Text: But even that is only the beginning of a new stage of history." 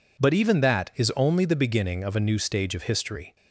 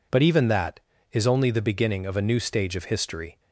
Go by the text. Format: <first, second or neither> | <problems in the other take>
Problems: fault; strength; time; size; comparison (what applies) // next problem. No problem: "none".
neither | none